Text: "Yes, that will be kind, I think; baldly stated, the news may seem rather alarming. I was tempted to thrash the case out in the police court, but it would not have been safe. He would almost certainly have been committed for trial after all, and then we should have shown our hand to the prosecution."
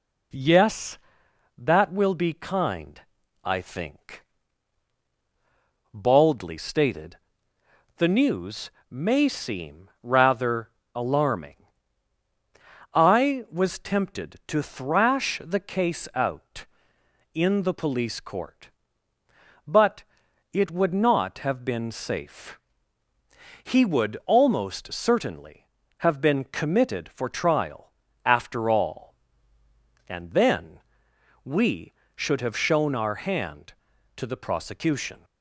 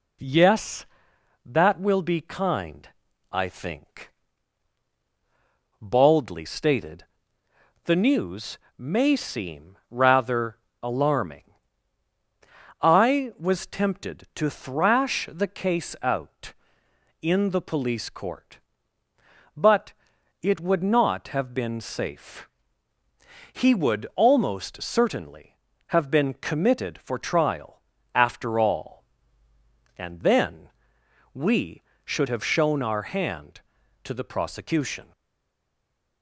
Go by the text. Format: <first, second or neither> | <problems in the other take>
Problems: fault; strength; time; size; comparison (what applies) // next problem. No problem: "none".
first | pauses between "news" and "may"; slight; at 8.5 s; 0.20 s long; slight in the first // pauses between "rather" and "alarming"; slight; at 10.5 s; 0.24 s long; slight in the first // pauses between "but" and "it"; noticeable; at 19.9 s; 0.48 s long; noticeable in the first // pauses between "trial" and "after"; slight; at 27.8 s; 0.32 s long; slight in the first // pauses between "then" and "we"; noticeable; at 30.6 s; 0.64 s long; noticeable in the first // stays silent after the last word; from 35.1 s on; 1.1 s long